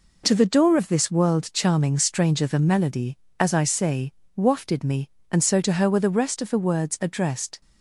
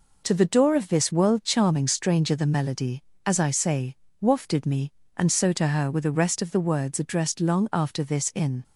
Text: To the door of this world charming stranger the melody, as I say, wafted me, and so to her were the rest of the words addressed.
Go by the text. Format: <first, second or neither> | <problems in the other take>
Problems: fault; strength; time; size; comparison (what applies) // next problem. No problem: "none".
first | goes on to say "Long after this in"; noticeable; from 7.4 s on; 1.2 s long